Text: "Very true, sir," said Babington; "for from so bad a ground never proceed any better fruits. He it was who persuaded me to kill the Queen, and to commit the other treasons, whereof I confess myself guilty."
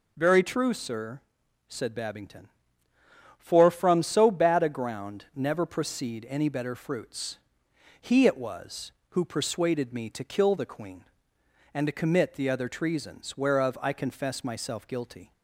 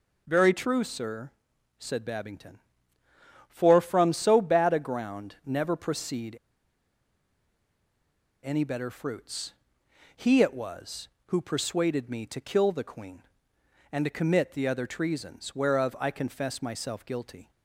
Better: first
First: none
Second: pauses between "proceed" and "any"; strong; at 6.3 s; 2.0 s long

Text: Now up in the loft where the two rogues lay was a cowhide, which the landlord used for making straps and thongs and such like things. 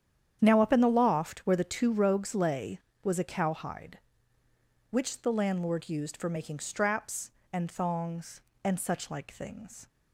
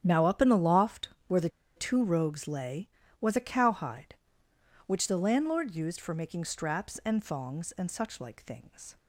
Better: first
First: starts louder than the rest; strong; until 1.4 s; 9 dB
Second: starts louder than the rest; strong; until 1.0 s; 9.5 dB // pauses between "loft" and "where"; slight; at 1.0 s; 0.18 s long // pauses between "the" and "two"; slight; at 1.4 s; 0.26 s long

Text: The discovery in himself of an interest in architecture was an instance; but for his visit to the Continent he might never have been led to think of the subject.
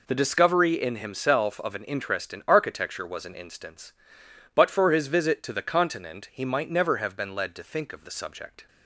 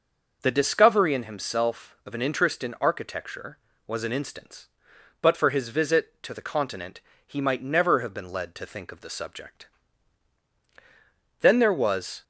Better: first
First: none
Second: starts louder than the rest; noticeable; until 1.4 s; 6 dB // pauses between "Continent" and "he"; slight; at 7.0 s; 0.26 s long // goes on to say "Then there was"; noticeable; from 11.4 s on; 0.82 s long

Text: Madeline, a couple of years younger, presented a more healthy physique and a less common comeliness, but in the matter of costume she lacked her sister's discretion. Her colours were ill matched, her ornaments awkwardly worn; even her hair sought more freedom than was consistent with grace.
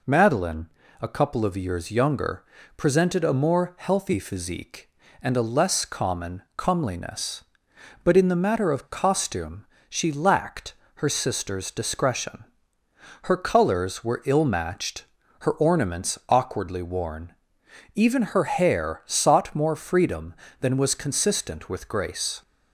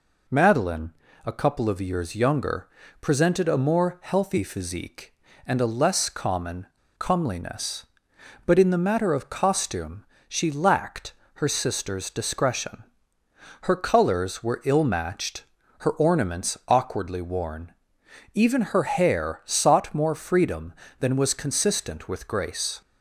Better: first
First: pauses between "costume" and "she"; slight; at 9.6 s; 0.24 s long // pauses between "lacked" and "her"; slight; at 10.7 s; 0.22 s long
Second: pauses between "common" and "comeliness"; slight; at 6.6 s; 0.31 s long // pauses between "costume" and "she"; slight; at 10.0 s; 0.24 s long // pauses between "lacked" and "her"; slight; at 11.1 s; 0.22 s long

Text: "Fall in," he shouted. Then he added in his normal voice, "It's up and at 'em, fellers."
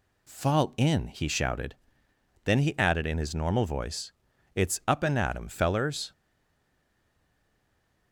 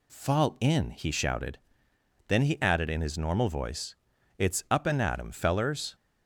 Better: second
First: stays silent after the last word; noticeable; from 6.1 s on; 2.0 s long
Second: none

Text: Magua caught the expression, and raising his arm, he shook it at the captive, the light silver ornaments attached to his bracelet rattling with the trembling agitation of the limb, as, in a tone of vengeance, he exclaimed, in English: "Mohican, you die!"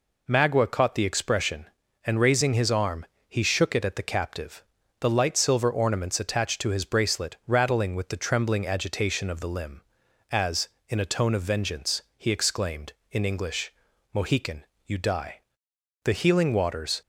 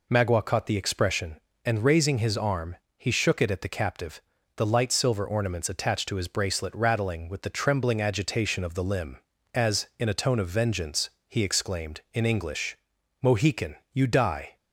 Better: second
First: goes on to say "The healing waters"; noticeable; from 16.0 s on; 0.96 s long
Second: none

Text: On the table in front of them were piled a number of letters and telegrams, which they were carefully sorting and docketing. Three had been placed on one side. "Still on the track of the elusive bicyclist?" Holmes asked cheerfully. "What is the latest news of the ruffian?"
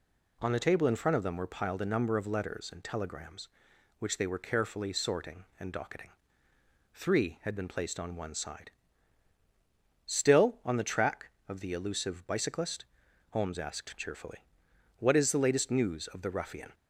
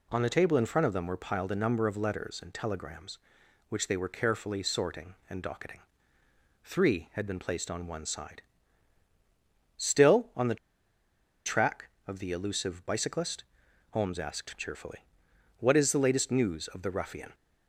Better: first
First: none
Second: pauses between "the" and "track"; noticeable; at 10.5 s; 0.90 s long

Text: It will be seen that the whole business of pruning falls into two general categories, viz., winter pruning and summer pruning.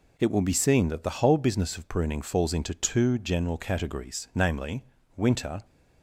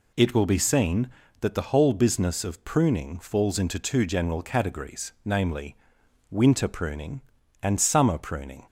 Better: second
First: stops before "pruning and summer pruning"; at 5.6 s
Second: none

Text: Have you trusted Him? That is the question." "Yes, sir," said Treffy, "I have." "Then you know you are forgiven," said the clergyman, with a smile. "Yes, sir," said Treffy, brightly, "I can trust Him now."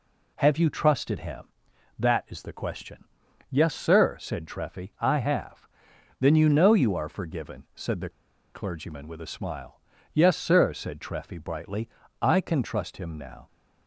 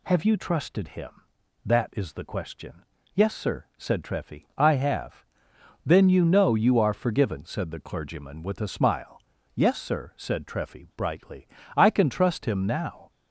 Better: second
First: pauses between "the" and "clergyman"; at 8.0 s; 0.45 s long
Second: none

